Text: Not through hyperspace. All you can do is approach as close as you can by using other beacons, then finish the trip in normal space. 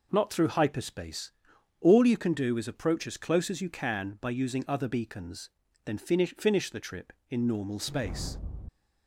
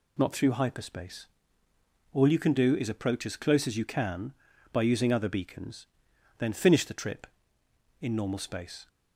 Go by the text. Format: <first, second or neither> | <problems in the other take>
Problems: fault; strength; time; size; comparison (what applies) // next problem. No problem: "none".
second | says "finish" twice; at 6.3 s